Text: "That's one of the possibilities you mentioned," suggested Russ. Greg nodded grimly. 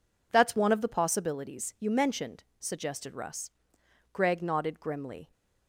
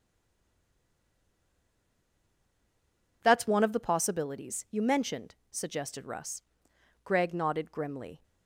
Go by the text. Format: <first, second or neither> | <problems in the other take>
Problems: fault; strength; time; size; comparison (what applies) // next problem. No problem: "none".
first | stays silent before the first word; strong; until 3.2 s; 3.2 s long